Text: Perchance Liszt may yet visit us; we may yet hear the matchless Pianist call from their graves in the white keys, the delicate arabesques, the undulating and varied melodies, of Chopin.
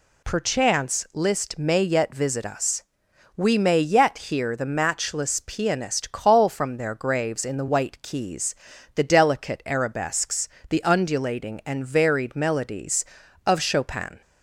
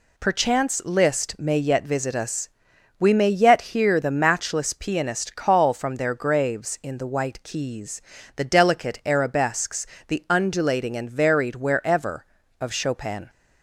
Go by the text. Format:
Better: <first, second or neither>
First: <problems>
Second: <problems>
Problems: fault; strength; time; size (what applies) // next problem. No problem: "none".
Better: first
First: none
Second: says "wherever" for "melodies"; at 11.5 s